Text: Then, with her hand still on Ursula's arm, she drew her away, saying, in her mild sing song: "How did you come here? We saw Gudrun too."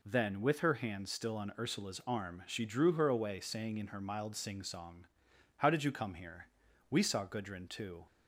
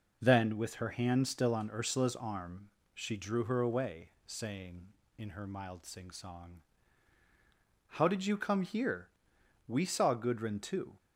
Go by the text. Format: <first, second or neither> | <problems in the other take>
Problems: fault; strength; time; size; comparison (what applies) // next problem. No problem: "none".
neither | none